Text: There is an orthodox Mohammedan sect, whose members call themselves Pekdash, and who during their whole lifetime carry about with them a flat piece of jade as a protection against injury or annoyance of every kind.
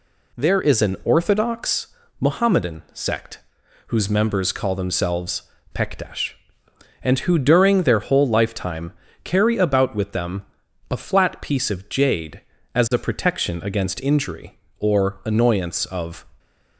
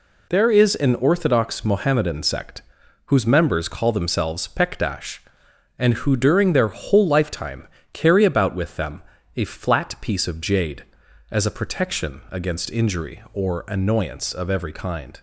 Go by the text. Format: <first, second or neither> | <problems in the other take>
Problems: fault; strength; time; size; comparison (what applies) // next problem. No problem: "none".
second | pauses between "orthodox" and "Mohammedan"; slight; at 1.8 s; 0.30 s long // pauses between "themselves" and "Pekdash"; slight; at 5.4 s; 0.34 s long // pauses between "lifetime" and "carry"; slight; at 8.9 s; 0.30 s long; slight in the second // pauses between "them" and "a"; noticeable; at 10.4 s; 0.46 s long; slight in the second // stops before "every kind"; at 16.3 s